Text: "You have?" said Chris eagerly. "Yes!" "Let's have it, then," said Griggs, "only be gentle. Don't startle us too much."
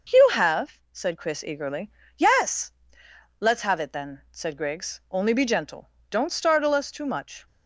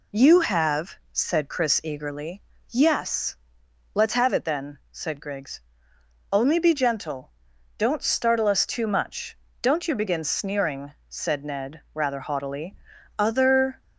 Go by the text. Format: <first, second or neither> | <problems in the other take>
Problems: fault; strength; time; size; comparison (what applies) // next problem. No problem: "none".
first | goes on to say "Don't you begin sneering said Ned rather haughtily Other"; strong; from 9.6 s on; 4.2 s long